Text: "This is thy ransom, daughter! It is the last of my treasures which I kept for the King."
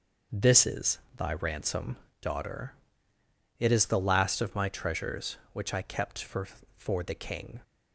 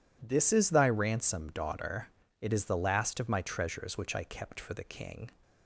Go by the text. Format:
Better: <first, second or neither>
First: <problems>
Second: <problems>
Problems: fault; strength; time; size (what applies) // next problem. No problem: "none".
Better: second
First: pauses between "is" and "thy"; slight; at 0.9 s; 0.18 s long // says "for" twice; at 6.7 s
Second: none